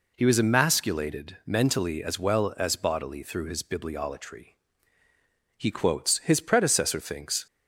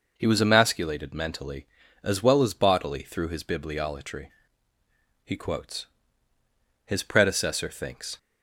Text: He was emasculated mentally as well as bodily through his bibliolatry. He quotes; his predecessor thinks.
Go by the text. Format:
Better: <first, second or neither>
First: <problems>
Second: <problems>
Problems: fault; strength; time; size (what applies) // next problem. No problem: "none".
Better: first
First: none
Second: changes voice at "was"; from 0.2 s on; 7.9 s long